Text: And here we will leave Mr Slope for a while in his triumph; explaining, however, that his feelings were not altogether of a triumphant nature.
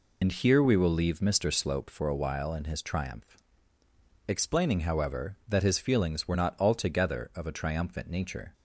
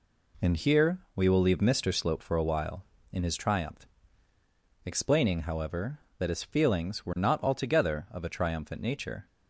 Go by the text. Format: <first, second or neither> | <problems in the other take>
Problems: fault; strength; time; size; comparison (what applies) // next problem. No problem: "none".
second | loses the start of "And"; at 0.2 s; 65 ms